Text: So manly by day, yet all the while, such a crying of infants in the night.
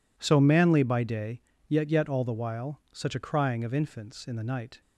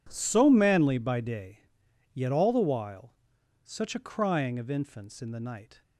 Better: second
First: says "yet" twice; at 1.9 s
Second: none

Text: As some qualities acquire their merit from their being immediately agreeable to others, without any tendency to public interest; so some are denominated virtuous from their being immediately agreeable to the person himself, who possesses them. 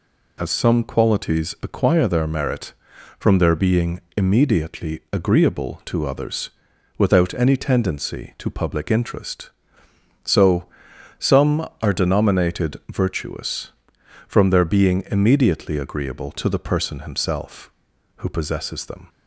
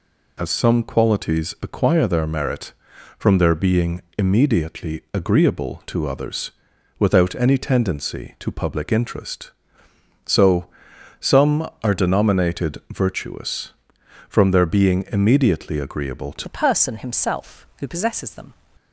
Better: first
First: pauses between "being" and "immediately"; slight; at 3.9 s; 0.16 s long // pauses between "so" and "some"; noticeable; at 10.6 s; 0.50 s long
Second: pauses between "being" and "immediately"; slight; at 4.0 s; 0.16 s long // pauses between "so" and "some"; noticeable; at 10.6 s; 0.50 s long // changes voice at "the"; from 16.4 s on; 2.1 s long

